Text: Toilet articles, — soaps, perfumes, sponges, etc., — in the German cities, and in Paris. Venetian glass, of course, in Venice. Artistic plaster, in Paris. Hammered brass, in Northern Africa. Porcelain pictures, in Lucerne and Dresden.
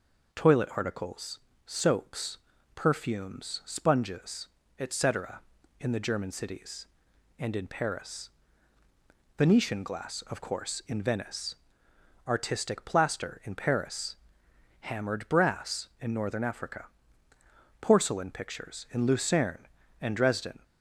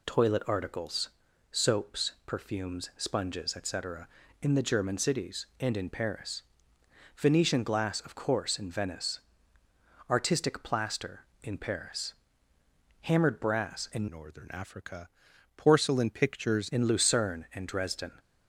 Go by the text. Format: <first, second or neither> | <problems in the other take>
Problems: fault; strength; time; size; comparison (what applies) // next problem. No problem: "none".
first | changes voice from "Northern" to "pictures"; from 14.1 to 16.7 s; 2.6 s long